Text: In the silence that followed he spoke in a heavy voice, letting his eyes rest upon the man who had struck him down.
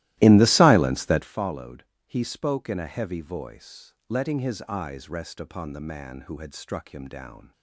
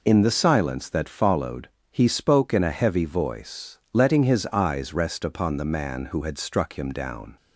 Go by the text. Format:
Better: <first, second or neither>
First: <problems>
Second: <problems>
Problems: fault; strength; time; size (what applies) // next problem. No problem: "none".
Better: second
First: starts louder than the rest; strong; until 1.4 s; 16.5 dB // pauses between "followed" and "he"; slight; at 1.8 s; 0.24 s long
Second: pauses between "followed" and "he"; slight; at 1.6 s; 0.24 s long